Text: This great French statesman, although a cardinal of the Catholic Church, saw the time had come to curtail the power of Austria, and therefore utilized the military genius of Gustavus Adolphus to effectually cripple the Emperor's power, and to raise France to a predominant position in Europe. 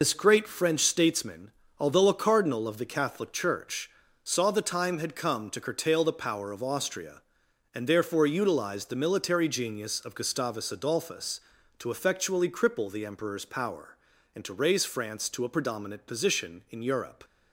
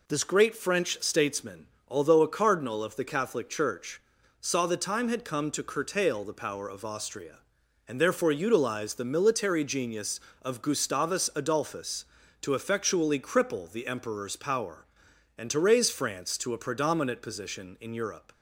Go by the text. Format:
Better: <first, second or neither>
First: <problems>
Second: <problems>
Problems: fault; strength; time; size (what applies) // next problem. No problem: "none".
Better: second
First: loses the start of "This"; at 0.0 s; 70 ms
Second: none